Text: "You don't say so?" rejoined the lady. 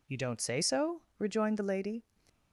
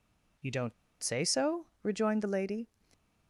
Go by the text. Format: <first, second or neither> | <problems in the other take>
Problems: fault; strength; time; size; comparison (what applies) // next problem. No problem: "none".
first | pauses between "don't" and "say"; slight; at 0.7 s; 0.30 s long